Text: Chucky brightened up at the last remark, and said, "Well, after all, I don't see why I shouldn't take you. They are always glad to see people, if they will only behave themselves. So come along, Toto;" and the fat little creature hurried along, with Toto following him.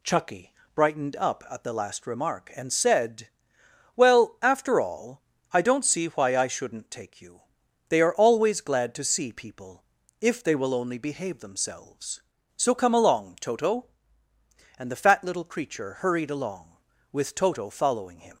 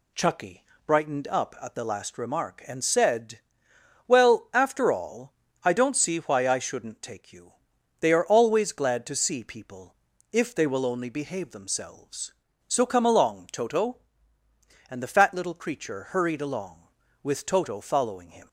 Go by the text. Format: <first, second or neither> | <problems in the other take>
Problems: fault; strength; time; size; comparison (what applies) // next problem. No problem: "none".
neither | pauses between "Chucky" and "brightened"; slight; the same in both